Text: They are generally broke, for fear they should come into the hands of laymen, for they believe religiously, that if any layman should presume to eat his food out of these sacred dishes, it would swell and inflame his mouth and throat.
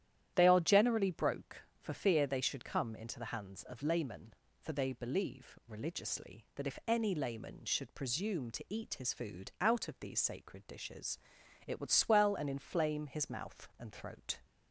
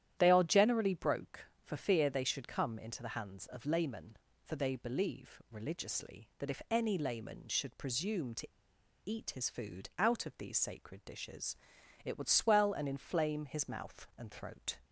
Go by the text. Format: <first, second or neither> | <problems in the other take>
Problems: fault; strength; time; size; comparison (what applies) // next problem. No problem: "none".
first | starts louder than the rest; strong; until 1.1 s; 11 dB; strong in the first // pauses between "to" and "eat"; noticeable; at 8.4 s; 0.57 s long